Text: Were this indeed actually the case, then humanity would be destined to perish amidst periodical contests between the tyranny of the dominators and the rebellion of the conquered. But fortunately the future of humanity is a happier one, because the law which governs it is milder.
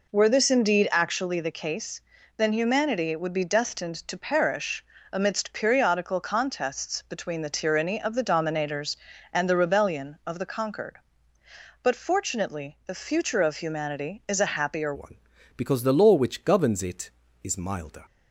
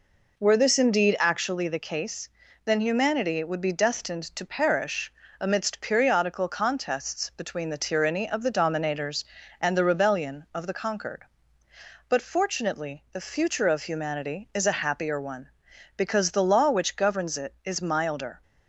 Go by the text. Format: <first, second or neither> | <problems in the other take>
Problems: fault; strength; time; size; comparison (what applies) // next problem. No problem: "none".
second | pauses between "perish" and "amidst"; slight; at 4.8 s; 0.30 s long; slight in the second // changes voice at "one"; from 14.9 s on; 3.1 s long